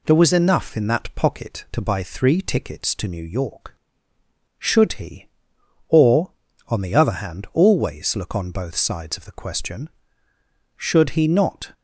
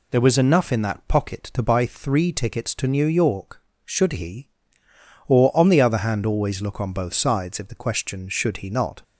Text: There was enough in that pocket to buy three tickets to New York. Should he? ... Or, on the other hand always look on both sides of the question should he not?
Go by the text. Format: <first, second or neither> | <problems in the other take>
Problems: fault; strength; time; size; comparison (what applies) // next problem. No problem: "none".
first | says "if" for "of"; at 7.5 s